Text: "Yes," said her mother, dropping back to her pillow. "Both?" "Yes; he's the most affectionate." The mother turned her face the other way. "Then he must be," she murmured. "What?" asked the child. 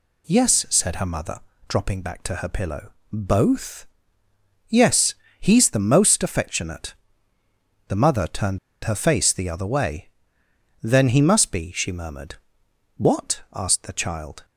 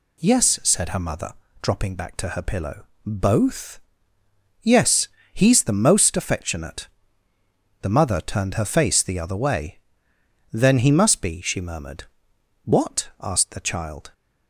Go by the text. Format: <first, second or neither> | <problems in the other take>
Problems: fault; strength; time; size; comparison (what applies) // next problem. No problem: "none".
second | pauses between "turned" and "her"; slight; at 8.5 s; 0.26 s long